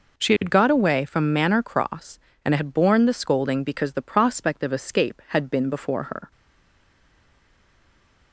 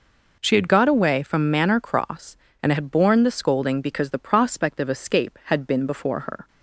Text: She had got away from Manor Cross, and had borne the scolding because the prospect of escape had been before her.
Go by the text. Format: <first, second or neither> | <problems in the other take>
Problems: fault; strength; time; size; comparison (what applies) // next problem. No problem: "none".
second | stays silent after the last word; noticeable; from 6.3 s on; 2.0 s long